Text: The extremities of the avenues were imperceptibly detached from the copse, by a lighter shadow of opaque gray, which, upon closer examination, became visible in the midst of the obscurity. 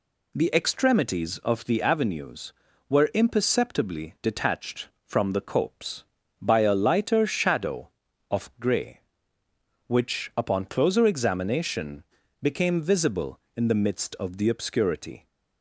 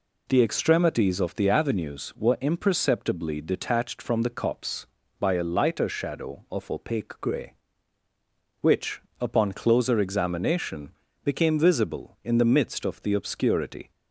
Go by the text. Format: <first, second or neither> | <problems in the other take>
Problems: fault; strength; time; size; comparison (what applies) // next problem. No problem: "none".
second | skips "opaque"; at 8.5 s